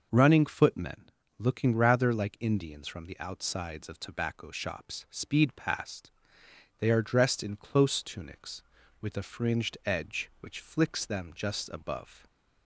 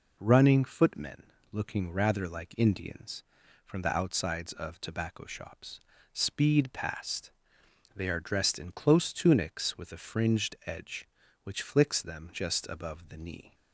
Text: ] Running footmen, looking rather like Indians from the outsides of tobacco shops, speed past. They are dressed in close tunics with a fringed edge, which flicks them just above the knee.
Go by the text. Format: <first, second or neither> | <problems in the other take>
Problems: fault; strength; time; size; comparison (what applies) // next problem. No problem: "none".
second | stops before "the knee"; at 12.2 s